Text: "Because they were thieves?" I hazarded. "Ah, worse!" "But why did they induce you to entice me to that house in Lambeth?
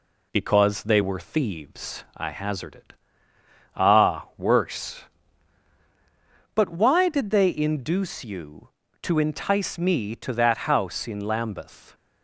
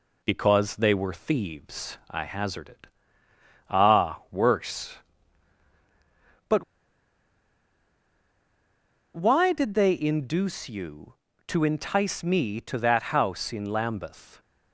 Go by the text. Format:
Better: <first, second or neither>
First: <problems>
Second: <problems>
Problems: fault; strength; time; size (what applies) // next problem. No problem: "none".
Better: first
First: none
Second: pauses between "But" and "why"; strong; at 6.6 s; 2.5 s long